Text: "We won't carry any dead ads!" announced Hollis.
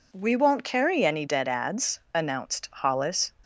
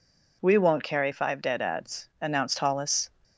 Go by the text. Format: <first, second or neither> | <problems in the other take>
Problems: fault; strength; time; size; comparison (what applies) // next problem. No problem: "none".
first | says "five" for "any"; at 1.1 s